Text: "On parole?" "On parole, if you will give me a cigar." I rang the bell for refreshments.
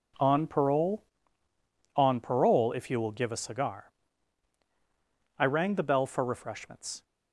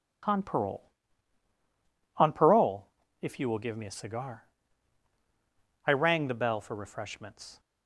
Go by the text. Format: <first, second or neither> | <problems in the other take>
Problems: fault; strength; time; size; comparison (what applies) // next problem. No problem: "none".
second | skips "me"; at 3.3 s